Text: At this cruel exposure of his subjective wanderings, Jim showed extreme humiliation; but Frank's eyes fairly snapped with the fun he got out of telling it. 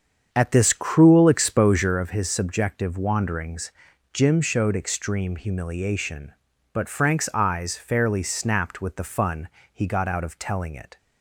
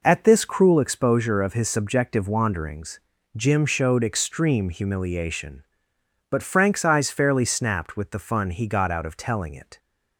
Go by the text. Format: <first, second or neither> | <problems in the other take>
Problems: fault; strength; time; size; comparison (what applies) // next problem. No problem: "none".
second | starts louder than the rest; strong; until 2.1 s; 7.5 dB // pauses between "fun" and "he"; slight; at 9.4 s; 0.24 s long